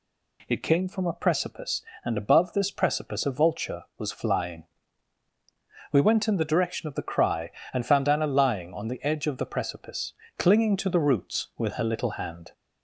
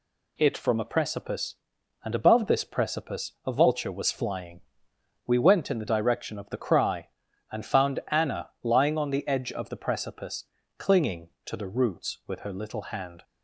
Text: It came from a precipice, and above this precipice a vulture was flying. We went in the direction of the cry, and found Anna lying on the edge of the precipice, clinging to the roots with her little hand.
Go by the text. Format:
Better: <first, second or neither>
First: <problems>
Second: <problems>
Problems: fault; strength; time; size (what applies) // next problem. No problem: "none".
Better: first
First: none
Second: skips "came"; at 0.5 s